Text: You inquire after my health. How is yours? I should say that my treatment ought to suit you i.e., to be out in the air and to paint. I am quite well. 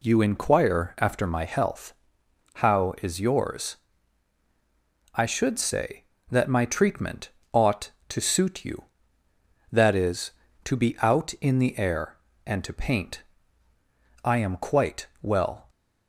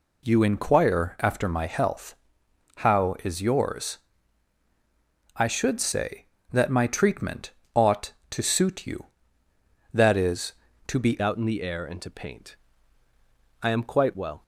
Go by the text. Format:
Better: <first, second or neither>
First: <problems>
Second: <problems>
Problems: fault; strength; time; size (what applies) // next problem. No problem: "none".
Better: first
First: pauses between "treatment" and "ought"; slight; at 7.3 s; 0.22 s long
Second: pauses between "treatment" and "ought"; slight; at 7.5 s; 0.22 s long // changes voice at "out"; from 11.2 s on; 3.2 s long